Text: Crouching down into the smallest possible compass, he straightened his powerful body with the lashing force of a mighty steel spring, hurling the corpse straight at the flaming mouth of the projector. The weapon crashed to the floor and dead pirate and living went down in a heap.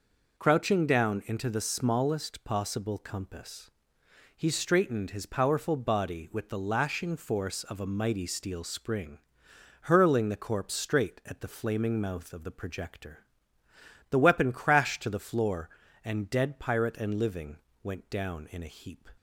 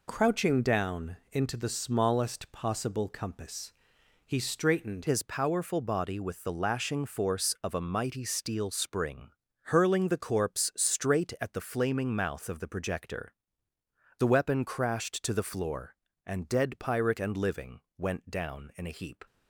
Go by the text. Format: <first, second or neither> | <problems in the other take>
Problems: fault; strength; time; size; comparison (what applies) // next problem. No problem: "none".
first | changes voice at "his"; from 5.0 s on; 14.2 s long // pauses between "living" and "went"; slight; at 17.7 s; 0.18 s long; slight in the first